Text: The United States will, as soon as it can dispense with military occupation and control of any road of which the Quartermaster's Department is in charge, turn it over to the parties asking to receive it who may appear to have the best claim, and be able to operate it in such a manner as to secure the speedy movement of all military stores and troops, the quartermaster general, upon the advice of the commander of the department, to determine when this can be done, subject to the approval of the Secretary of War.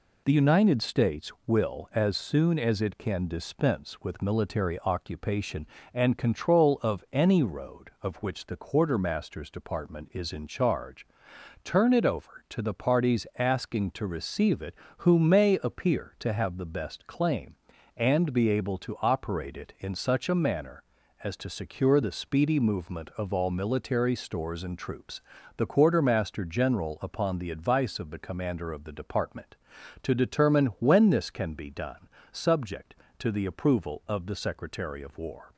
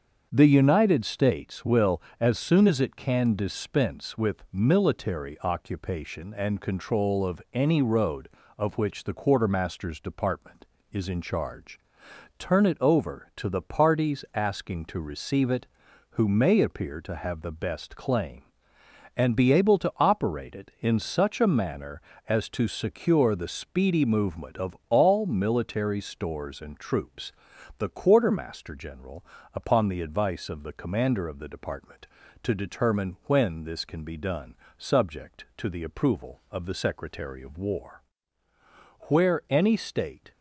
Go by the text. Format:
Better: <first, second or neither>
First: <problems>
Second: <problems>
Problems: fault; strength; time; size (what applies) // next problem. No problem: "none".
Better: first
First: none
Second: starts louder than the rest; until 1.3 s; 7 dB // goes on to say "Where any State"; noticeable; from 39.0 s on; 1.2 s long